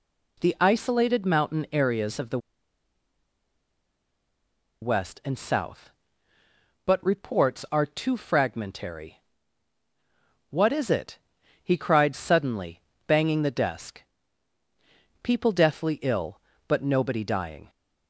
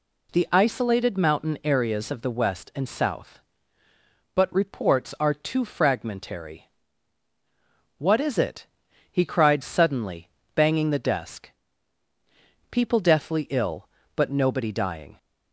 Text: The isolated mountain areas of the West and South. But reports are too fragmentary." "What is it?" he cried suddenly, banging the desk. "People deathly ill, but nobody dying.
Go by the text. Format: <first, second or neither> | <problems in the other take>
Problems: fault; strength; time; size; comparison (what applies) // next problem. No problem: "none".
second | pauses between "the" and "West"; strong; at 2.3 s; 2.4 s long